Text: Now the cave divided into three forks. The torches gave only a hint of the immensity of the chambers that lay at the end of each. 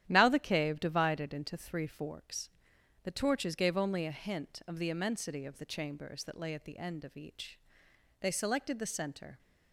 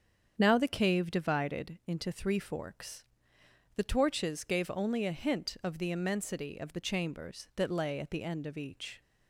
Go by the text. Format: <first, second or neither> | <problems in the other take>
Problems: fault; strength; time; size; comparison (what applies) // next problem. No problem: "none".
second | starts louder than the rest; strong; until 1.0 s; 11 dB; strong in the second // goes on to say "They selected the center"; noticeable; from 8.1 s on; 1.1 s long